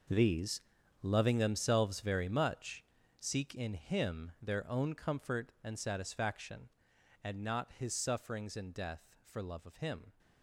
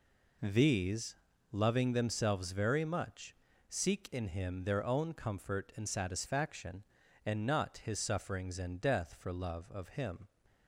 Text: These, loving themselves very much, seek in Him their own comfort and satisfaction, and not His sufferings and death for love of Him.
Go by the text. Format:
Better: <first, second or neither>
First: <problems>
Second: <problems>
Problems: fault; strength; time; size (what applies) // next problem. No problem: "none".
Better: second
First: gets quieter; strong; throughout; 15 dB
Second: none